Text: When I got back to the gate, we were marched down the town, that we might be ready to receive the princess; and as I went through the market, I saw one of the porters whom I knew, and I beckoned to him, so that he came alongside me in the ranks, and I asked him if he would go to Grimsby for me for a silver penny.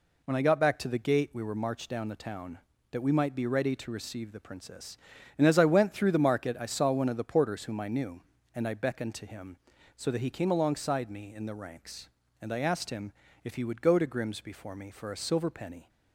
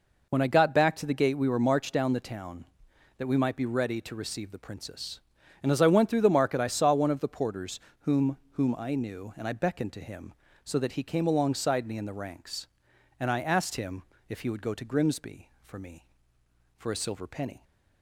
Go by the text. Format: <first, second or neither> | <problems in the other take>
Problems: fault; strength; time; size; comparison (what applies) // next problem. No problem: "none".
first | pauses between "porters" and "whom"; slight; at 7.7 s; 0.22 s long // says "whom" twice; at 8.5 s // pauses between "him" and "if"; slight; at 14.0 s; 0.26 s long; slight in the first